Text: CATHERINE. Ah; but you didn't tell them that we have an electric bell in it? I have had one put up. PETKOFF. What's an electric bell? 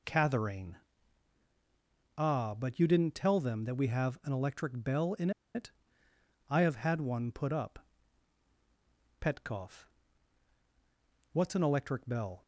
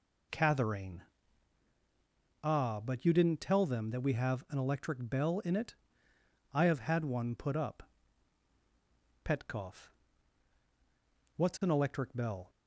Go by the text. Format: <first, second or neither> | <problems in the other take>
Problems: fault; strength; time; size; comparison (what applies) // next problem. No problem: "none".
second | pauses between "in" and "it"; slight; at 5.2 s; 0.25 s long